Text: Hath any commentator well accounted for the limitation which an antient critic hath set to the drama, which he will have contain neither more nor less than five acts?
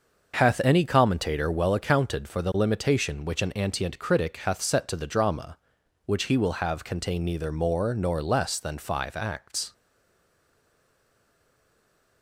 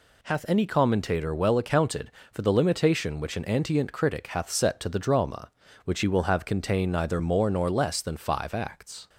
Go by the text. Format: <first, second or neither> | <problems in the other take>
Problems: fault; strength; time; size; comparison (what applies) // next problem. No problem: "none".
second | starts louder than the rest; noticeable; until 1.4 s; 6 dB // stays silent after the last word; from 9.7 s on; 2.5 s long